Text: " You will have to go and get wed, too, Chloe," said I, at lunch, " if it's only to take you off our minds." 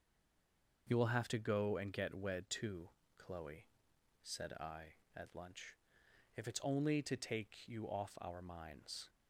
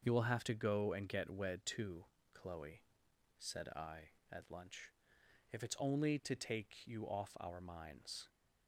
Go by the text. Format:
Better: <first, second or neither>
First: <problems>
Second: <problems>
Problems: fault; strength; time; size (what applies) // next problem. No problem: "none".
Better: second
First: stays silent before the first word; slight; until 0.8 s; 0.8 s long // starts louder than the rest; until 1.9 s; 6.5 dB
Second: starts louder than the rest; until 1.0 s; 6.5 dB